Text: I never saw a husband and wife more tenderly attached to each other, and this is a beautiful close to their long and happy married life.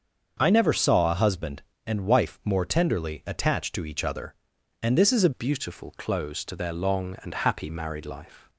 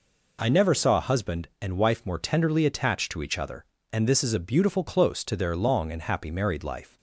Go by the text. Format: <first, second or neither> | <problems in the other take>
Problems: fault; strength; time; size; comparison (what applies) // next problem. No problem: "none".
second | starts louder than the rest; until 1.4 s; 7 dB // changes voice at "beautiful"; from 5.3 s on; 3.1 s long